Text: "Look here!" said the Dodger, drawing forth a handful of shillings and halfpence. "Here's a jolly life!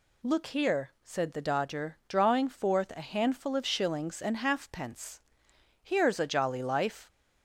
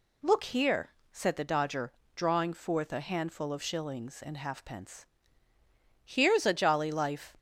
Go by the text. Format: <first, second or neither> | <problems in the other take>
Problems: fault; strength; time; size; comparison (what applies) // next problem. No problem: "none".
neither | none